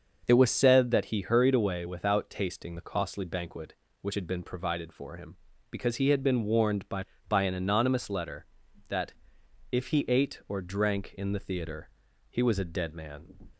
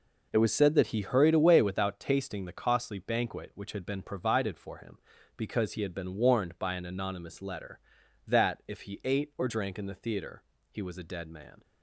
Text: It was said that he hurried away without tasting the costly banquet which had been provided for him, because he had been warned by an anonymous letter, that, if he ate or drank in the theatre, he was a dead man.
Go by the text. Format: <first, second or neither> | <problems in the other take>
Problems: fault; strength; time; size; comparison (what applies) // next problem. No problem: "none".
second | starts louder than the rest; noticeable; until 1.2 s; 6 dB // says "by" twice; at 7.2 s